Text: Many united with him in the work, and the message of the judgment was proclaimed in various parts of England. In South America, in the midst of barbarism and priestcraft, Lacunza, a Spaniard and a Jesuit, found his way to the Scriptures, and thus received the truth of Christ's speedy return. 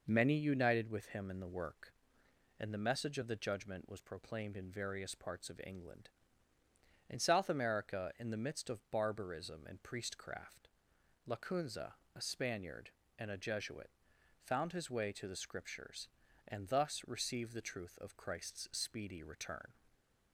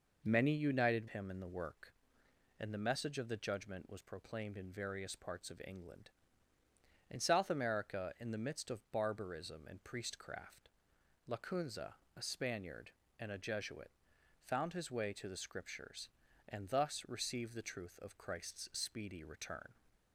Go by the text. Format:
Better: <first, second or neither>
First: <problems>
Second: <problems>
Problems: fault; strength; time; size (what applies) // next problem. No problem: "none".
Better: first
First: none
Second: skips "with"; at 1.0 s